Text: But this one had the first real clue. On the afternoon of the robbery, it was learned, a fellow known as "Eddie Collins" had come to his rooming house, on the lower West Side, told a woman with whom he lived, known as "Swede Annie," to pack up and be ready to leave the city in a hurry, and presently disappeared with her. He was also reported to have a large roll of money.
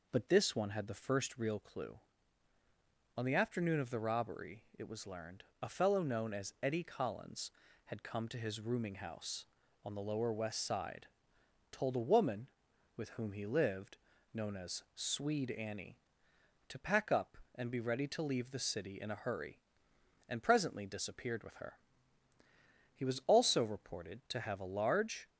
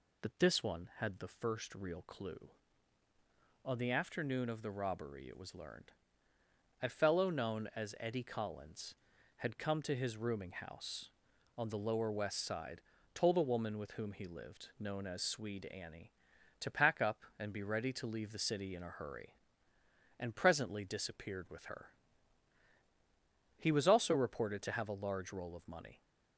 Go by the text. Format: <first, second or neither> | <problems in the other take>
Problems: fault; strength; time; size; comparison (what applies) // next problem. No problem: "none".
second | stops before "roll of money"; at 25.2 s